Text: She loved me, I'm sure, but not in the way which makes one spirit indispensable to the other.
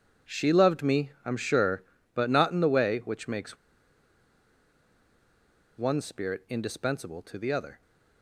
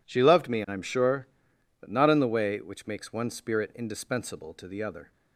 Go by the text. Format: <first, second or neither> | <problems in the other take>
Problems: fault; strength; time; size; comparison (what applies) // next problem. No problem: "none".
second | pauses between "makes" and "one"; strong; at 3.5 s; 2.2 s long